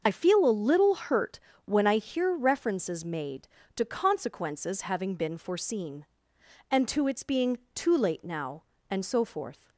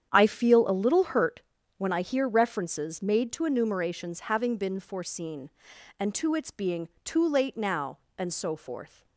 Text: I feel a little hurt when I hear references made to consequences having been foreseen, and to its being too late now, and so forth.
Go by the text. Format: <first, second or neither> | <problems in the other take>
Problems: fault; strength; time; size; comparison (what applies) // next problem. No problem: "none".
first | starts louder than the rest; strong; until 1.1 s; 9 dB; also in the first // pauses between "hurt" and "when"; slight; at 1.4 s; 0.36 s long; slight in the first // says "enumerations" for "consequences"; at 3.4 s // pauses between "being" and "too"; slight; at 6.8 s; 0.16 s long; slight in the first